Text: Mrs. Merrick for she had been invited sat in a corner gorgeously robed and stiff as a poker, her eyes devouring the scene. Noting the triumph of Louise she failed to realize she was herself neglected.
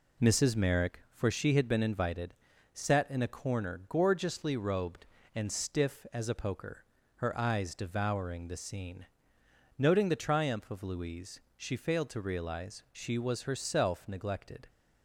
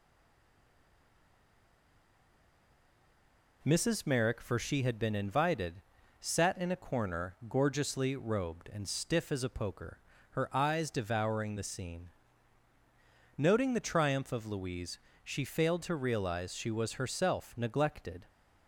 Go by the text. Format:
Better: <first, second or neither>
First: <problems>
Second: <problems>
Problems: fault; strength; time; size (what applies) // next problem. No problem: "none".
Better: first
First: pauses between "invited" and "sat"; at 2.3 s; 0.40 s long // pauses between "Louise" and "she"; slight; at 11.3 s; 0.16 s long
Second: stays silent before the first word; strong; until 3.6 s; 3.6 s long // pauses between "invited" and "sat"; slight; at 5.8 s; 0.36 s long // pauses between "Louise" and "she"; slight; at 14.9 s; 0.28 s long